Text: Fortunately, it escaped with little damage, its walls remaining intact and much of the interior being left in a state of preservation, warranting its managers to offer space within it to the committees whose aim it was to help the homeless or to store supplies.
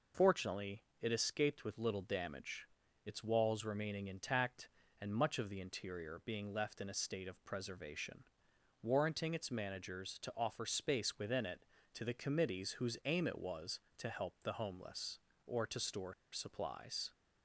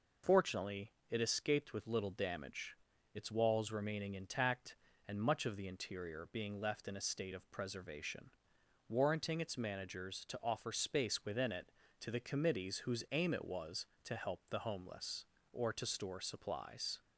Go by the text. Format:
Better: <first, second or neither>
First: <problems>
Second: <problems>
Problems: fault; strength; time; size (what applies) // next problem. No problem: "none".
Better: second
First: pauses between "store" and "supplies"; slight; at 16.1 s; 0.18 s long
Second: none